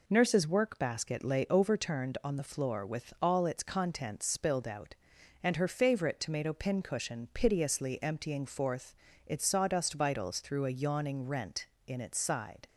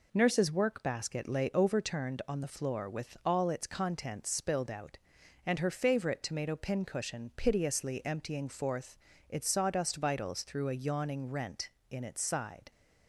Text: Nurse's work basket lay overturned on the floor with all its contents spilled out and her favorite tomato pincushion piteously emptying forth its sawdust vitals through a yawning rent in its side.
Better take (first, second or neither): neither